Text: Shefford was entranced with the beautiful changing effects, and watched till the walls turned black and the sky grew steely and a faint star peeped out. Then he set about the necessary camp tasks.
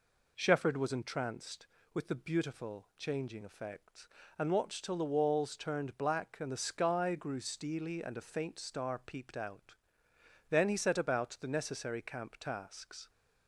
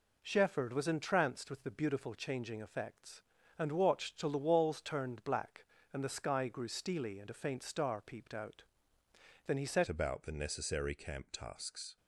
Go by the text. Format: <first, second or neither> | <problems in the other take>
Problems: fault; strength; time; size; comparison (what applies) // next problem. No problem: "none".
first | changes voice at "about"; from 9.8 s on; 2.1 s long